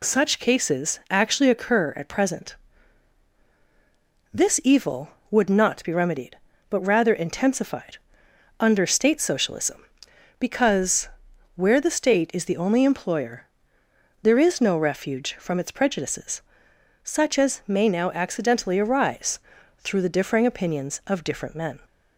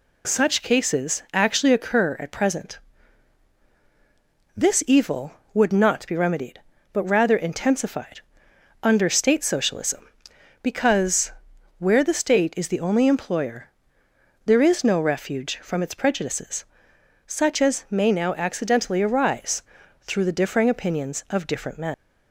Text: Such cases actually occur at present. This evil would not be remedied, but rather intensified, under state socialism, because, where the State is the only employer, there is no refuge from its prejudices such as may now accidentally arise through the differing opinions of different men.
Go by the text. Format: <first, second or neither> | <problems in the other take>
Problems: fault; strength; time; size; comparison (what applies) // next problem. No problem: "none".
first | pauses between "prejudices" and "such"; noticeable; at 16.6 s; 0.64 s long; noticeable in the first // pauses between "arise" and "through"; at 19.6 s; 0.40 s long; also in the first // leaves "men" unfinished; at 21.9 s; 140 ms